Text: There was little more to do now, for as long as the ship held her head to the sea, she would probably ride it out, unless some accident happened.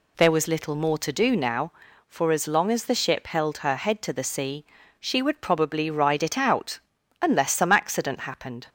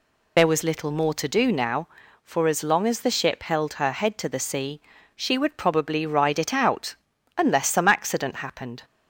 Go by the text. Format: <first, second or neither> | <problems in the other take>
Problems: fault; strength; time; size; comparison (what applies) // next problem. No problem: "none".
first | loses the start of "There"; at 0.3 s; 45 ms